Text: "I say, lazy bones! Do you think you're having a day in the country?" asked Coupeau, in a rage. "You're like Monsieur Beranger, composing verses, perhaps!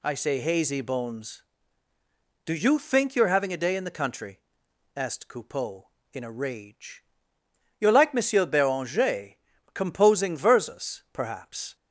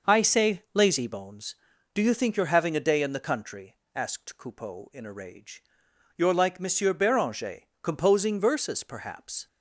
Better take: second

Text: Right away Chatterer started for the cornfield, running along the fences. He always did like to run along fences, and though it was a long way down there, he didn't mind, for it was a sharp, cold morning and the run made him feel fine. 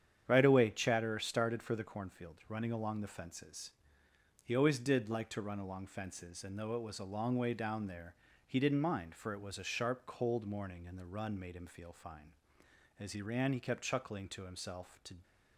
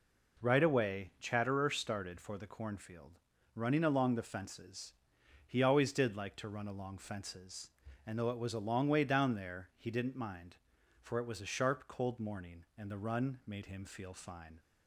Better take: second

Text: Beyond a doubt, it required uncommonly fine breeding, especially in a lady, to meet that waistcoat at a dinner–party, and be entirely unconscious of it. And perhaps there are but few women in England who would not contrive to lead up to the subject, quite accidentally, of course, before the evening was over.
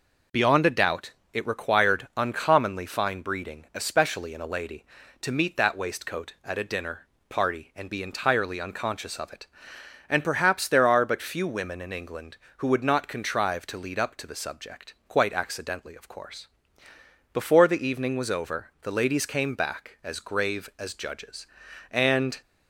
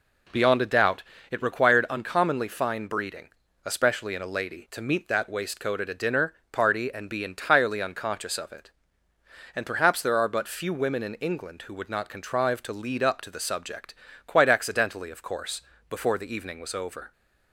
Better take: second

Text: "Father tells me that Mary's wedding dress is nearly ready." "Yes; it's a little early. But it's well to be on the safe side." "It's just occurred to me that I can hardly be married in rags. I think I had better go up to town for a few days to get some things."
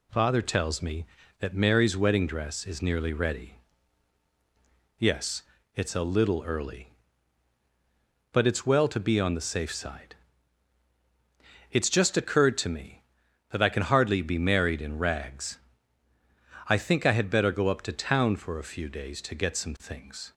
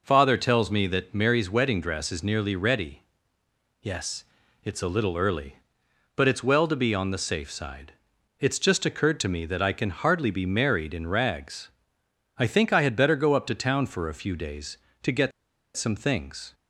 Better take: first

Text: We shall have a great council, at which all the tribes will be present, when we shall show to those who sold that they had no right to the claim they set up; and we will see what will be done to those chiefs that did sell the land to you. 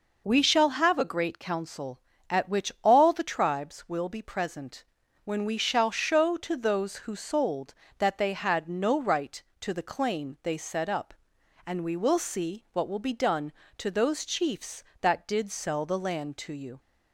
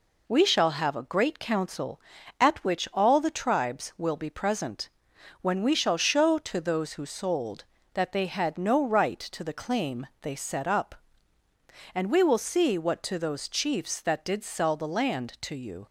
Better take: first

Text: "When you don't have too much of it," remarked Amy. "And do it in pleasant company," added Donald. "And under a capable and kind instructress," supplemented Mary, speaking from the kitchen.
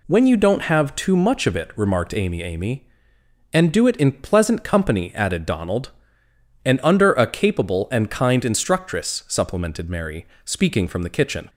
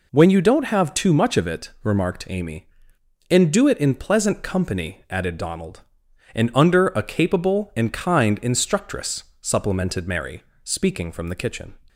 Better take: second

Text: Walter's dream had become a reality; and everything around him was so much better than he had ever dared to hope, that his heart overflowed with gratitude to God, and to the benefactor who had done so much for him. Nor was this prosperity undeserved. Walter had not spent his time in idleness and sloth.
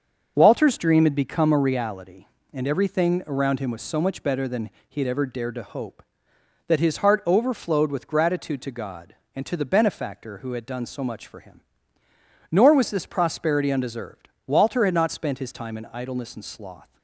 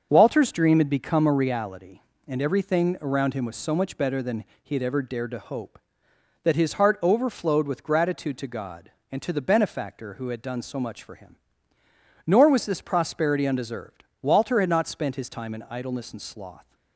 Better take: neither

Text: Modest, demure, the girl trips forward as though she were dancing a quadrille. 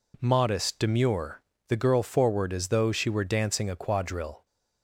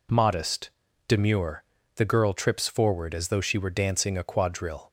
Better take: second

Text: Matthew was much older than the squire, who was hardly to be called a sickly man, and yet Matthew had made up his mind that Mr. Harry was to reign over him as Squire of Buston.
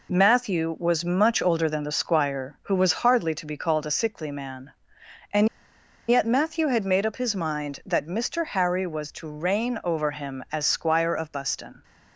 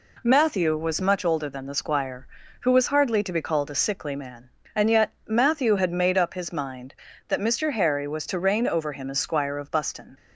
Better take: second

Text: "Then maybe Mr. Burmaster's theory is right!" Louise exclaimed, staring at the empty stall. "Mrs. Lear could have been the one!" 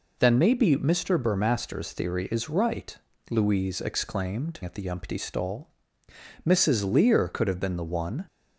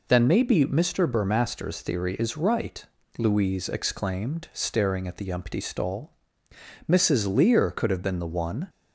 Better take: second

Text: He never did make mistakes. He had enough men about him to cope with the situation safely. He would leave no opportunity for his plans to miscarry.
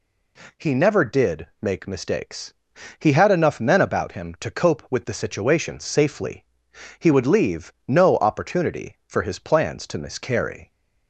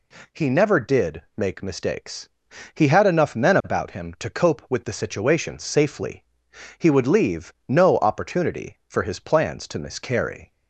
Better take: neither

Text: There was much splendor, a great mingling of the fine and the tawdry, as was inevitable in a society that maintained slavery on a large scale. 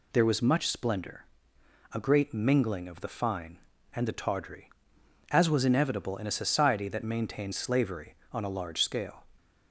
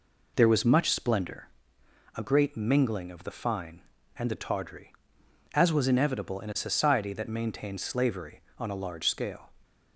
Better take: first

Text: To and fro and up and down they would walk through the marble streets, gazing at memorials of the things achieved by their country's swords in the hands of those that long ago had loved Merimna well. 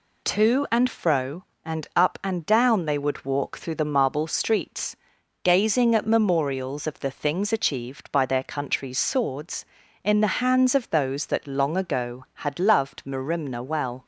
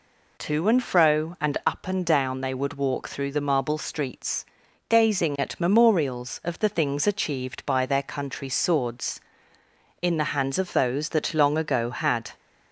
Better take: first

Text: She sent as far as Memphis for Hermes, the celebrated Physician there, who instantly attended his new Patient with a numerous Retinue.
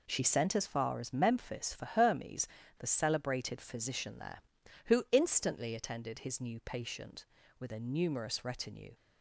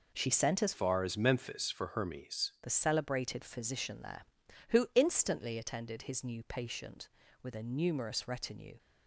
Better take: first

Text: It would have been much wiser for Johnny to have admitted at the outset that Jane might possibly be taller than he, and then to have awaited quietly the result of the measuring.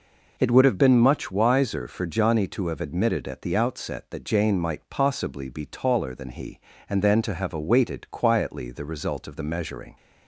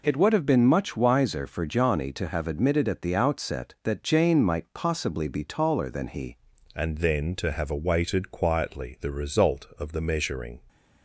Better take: first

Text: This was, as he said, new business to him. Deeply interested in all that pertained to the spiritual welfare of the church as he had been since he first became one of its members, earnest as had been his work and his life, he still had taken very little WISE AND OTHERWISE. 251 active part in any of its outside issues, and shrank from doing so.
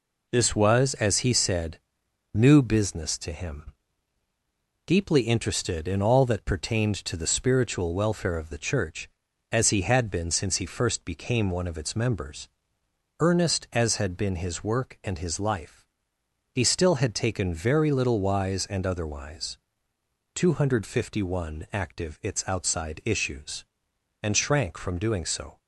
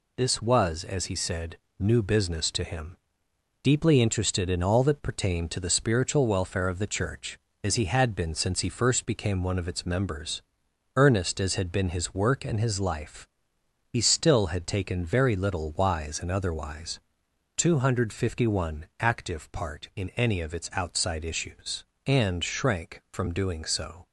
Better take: second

